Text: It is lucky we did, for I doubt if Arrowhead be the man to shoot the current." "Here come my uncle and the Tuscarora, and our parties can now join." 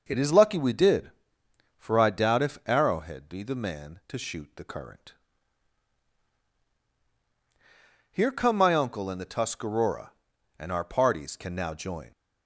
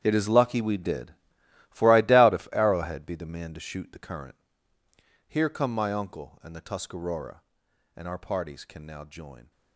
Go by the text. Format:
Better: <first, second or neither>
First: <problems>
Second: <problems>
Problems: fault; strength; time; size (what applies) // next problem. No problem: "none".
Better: first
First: none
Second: gets quieter; strong; throughout; 15 dB